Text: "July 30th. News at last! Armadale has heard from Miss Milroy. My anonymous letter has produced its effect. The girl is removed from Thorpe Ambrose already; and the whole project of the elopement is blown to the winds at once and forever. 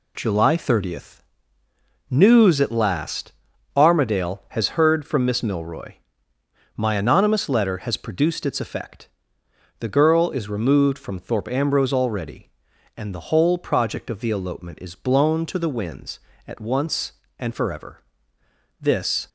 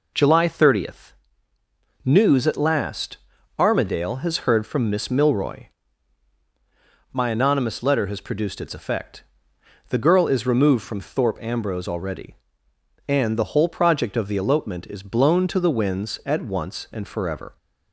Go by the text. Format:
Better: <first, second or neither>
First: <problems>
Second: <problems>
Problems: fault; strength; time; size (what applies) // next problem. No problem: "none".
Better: second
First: goes on to say "This"; slight; from 18.8 s on; 0.48 s long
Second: none